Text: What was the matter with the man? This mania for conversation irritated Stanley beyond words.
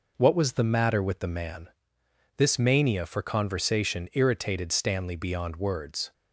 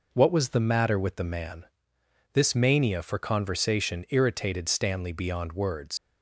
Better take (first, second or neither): first